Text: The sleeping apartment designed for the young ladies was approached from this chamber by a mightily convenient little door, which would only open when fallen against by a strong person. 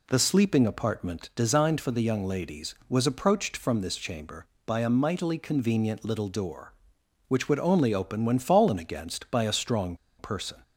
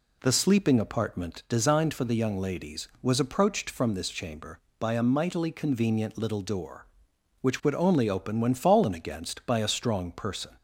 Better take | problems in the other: second | pauses between "strong" and "person"; slight; at 9.9 s; 0.23 s long

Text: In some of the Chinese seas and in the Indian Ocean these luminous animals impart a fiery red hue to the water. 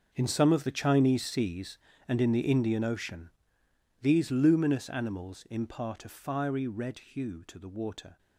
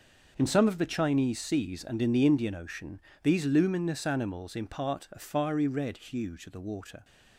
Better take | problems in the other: second | gets quieter; strong; throughout; 15 dB // pauses between "Ocean" and "these"; noticeable; at 3.2 s; 0.72 s long; slight in the second

